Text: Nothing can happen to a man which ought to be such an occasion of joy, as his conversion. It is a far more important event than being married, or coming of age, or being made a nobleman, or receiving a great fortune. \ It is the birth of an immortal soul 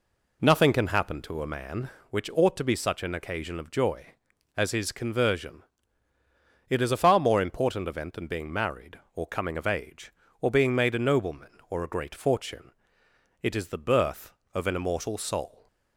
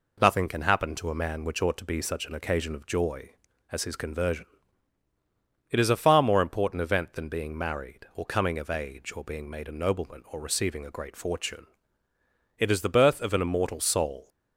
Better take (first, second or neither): second